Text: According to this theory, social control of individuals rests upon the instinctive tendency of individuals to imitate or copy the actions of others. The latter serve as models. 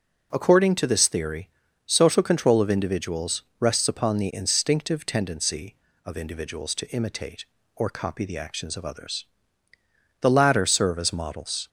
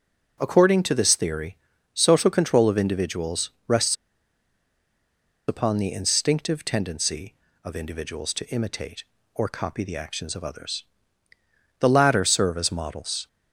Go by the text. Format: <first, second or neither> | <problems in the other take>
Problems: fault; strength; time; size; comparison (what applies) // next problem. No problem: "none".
first | pauses between "individuals" and "rests"; slight; at 3.5 s; 0.16 s long; slight in the first // pauses between "rests" and "upon"; strong; at 3.9 s; 1.5 s long